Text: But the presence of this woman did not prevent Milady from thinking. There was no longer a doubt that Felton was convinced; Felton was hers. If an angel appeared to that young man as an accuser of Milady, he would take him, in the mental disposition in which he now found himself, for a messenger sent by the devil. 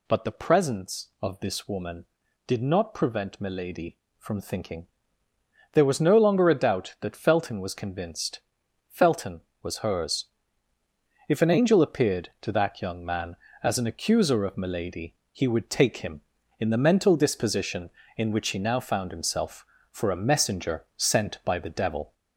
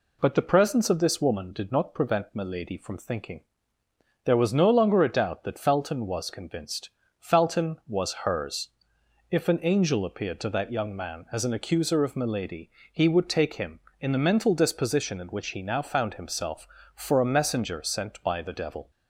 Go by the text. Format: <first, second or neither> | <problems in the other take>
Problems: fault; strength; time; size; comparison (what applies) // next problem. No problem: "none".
second | gets louder; throughout; 3.5 dB